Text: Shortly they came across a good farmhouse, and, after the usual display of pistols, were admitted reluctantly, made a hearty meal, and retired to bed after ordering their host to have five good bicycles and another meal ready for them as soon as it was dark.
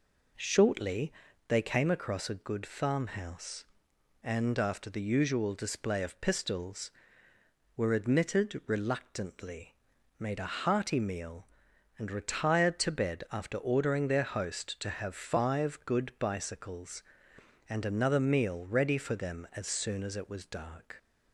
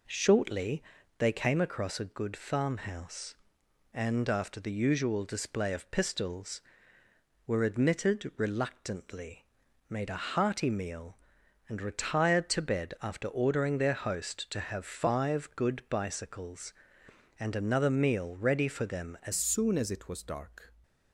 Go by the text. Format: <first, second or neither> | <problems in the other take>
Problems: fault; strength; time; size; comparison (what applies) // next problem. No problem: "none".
first | pauses between "Shortly" and "they"; slight; at 0.8 s; 0.36 s long; slight in the first // changes voice at "soon"; from 19.3 s on; 1.4 s long